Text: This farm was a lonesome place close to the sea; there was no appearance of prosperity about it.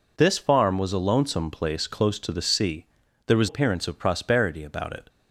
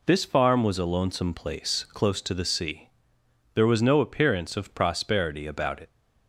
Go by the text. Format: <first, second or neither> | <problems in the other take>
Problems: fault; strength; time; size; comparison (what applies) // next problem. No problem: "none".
second | skips "no"; at 3.4 s